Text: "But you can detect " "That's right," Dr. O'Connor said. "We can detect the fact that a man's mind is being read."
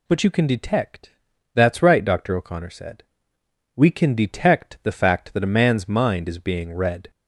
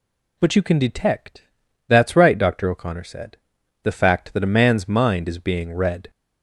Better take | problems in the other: first | skips "We can detect"; at 3.6 s

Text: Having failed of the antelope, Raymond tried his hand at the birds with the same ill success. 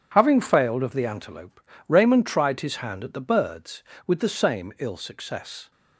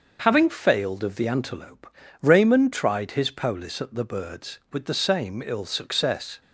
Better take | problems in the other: first | starts louder than the rest; until 1.2 s; 6.5 dB // says "polis" for "hand"; at 3.3 s

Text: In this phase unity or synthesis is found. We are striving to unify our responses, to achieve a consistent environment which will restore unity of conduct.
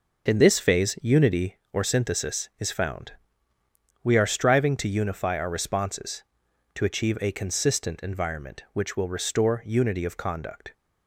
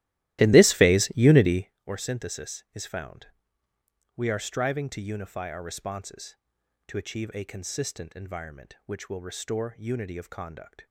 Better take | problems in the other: first | starts louder than the rest; strong; until 1.8 s; 15.5 dB

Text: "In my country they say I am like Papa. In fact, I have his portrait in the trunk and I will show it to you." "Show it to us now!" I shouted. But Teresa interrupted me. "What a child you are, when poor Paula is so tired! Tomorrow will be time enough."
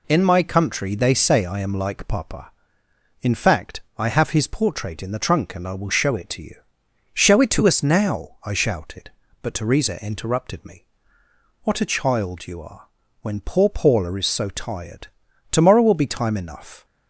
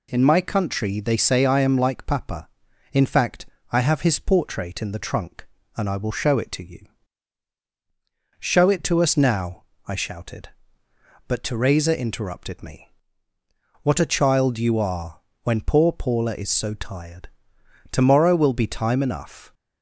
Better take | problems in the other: neither | none

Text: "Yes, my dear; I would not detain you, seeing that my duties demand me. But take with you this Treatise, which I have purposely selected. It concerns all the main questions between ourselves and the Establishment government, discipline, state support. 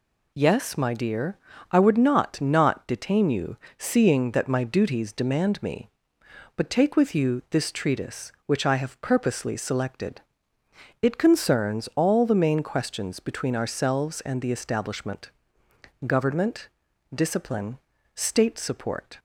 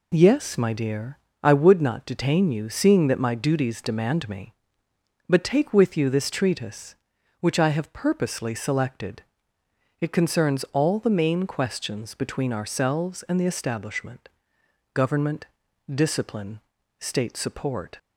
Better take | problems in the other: second | says "not" twice; at 2.3 s // pauses between "Establishment" and "government"; noticeable; at 15.3 s; 0.76 s long; noticeable in the second

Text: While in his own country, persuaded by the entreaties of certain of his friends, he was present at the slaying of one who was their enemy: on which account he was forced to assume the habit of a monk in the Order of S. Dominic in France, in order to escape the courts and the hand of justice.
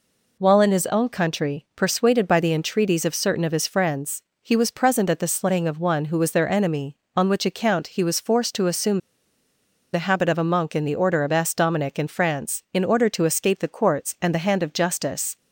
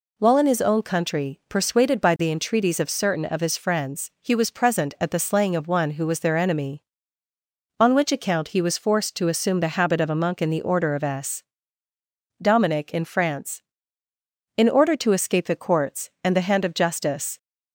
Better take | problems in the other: second | pauses between "assume" and "the"; noticeable; at 8.9 s; 0.93 s long

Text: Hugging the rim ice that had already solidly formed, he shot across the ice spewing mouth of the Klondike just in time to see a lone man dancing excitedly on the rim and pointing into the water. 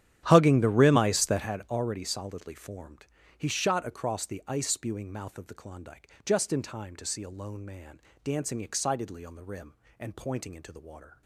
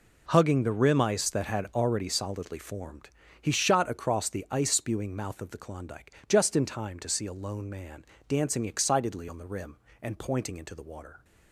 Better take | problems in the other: second | starts louder than the rest; strong; until 1.5 s; 10.5 dB // pauses between "Klondike" and "just"; slight; at 6.0 s; 0.16 s long; slight in the second // pauses between "man" and "dancing"; slight; at 7.9 s; 0.24 s long; slight in the second

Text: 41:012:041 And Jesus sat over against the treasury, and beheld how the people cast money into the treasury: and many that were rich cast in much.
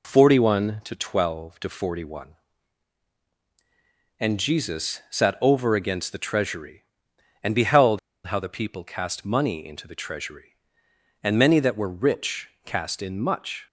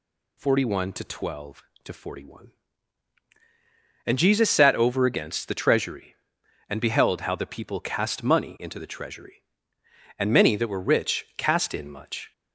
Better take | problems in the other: second | pauses between "beheld" and "how"; slight; at 7.9 s; 0.27 s long // pauses between "rich" and "cast"; slight; at 12.4 s; 0.16 s long

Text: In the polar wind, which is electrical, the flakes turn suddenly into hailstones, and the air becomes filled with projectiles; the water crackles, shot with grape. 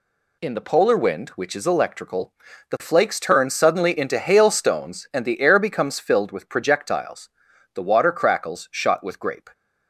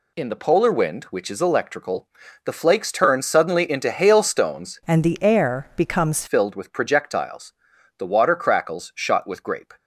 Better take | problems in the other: first | changes voice from "and" to "becomes"; from 4.8 to 6.2 s; 1.4 s long

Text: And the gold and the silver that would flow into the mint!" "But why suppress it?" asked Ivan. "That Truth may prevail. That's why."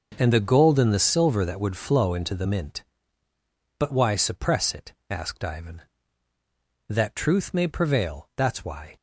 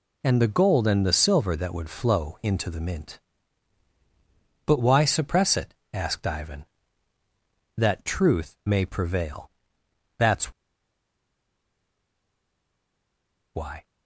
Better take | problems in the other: first | pauses between "That's" and "why"; strong; at 10.5 s; 3.0 s long

